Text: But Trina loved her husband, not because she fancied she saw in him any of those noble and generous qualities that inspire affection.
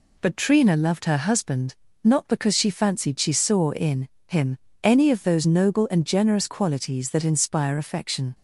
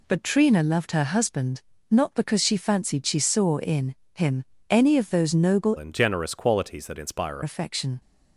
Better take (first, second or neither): first